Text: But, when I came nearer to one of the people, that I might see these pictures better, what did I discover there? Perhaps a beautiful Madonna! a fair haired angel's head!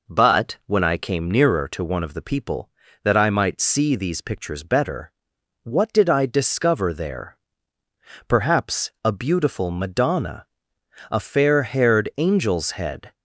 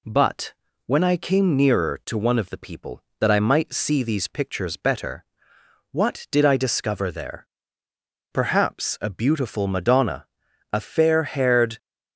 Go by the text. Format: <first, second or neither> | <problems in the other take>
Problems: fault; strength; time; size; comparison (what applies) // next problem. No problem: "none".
first | stops before "angel's head"; at 11.7 s